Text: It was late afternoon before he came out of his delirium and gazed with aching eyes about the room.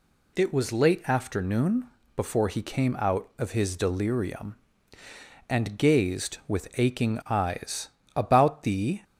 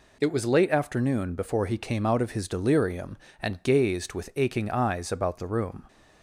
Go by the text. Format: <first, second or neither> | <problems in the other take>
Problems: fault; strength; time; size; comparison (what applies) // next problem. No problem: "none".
second | pauses between "afternoon" and "before"; slight; at 1.8 s; 0.28 s long // pauses between "eyes" and "about"; slight; at 7.8 s; 0.28 s long // stops before "room"; at 9.0 s